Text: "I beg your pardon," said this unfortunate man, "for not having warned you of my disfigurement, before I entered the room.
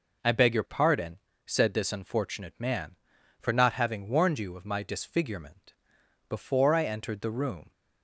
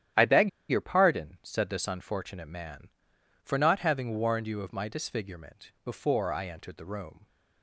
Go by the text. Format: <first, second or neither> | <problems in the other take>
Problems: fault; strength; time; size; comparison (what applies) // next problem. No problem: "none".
first | starts louder than the rest; strong; until 1.3 s; 11 dB // pauses between "beg" and "your"; slight; at 0.4 s; 0.21 s long